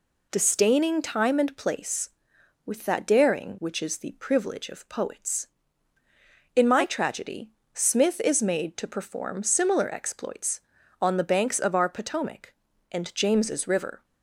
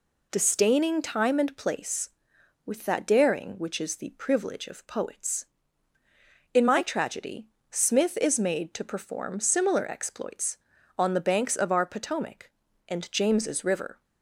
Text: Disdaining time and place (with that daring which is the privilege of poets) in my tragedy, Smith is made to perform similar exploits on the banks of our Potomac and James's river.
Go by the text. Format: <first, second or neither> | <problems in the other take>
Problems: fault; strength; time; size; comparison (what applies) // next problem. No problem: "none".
neither | none